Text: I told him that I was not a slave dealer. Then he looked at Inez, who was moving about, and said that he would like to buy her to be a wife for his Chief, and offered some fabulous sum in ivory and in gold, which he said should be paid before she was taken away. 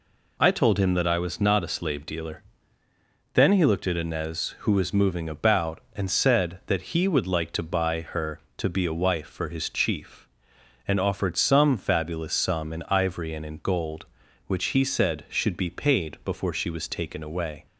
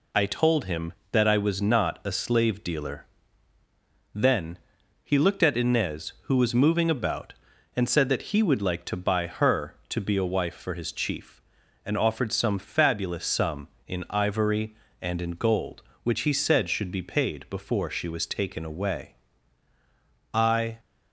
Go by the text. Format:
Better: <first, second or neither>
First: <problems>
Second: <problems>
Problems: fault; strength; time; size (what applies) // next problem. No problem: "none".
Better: first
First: none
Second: pauses between "Then" and "he"; noticeable; at 4.5 s; 0.46 s long // goes on to say "I"; slight; from 20.3 s on; 0.46 s long